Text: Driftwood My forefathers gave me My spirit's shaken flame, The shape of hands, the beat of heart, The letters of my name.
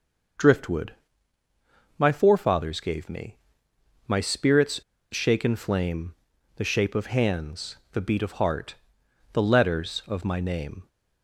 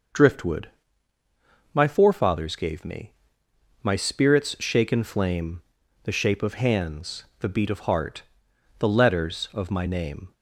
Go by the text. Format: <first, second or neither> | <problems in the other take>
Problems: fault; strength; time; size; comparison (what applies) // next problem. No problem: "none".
second | pauses between "Driftwood" and "My"; at 0.9 s; 1.0 s long; also in the second // pauses between "me" and "My"; noticeable; at 3.3 s; 0.68 s long; noticeable in the second // pauses between "spirit's" and "shaken"; slight; at 4.7 s; 0.32 s long